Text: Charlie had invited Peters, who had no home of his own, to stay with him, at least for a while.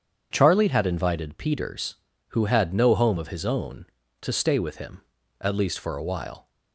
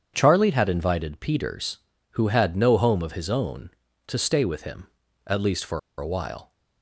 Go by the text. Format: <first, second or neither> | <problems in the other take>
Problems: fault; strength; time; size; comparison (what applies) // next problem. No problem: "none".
first | starts louder than the rest; strong; until 1.1 s; 8 dB; strong in the first // pauses between "for" and "a"; slight; at 5.7 s; 0.20 s long